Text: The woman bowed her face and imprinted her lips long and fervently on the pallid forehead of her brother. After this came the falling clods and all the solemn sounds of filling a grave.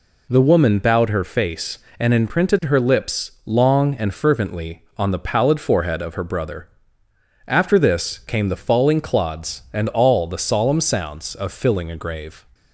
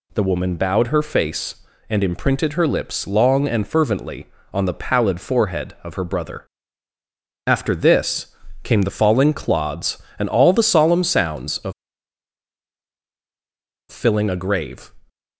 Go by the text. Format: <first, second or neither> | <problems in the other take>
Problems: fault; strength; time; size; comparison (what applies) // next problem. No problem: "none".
first | pauses between "this" and "came"; slight; at 8.2 s; 0.36 s long // pauses between "of" and "filling"; strong; at 11.7 s; 2.1 s long